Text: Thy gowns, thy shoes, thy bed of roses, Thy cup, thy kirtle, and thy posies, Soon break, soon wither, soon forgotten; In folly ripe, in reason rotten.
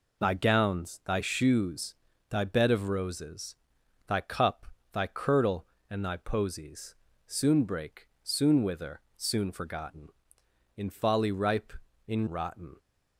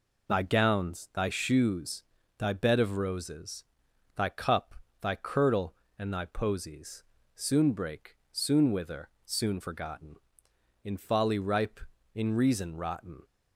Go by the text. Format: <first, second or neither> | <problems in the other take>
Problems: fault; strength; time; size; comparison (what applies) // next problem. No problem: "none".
second | skips "reason"; at 12.2 s